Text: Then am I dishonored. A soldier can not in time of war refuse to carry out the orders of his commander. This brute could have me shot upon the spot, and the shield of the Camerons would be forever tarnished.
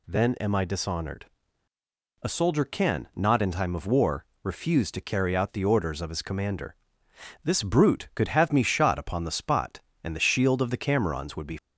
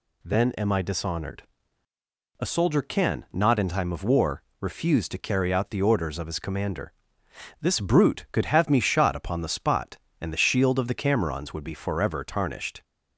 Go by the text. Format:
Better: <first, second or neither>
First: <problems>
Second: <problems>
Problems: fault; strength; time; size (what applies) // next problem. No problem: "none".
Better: second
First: pauses between "war" and "refuse"; slight; at 4.2 s; 0.16 s long // stops before "forever tarnished"; at 11.5 s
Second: pauses between "war" and "refuse"; slight; at 4.4 s; 0.16 s long